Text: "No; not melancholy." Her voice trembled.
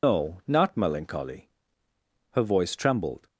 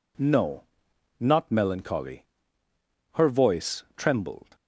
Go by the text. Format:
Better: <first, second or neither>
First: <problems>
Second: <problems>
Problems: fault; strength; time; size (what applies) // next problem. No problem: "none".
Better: second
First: loses the start of "No"; at 0.0 s; 160 ms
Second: none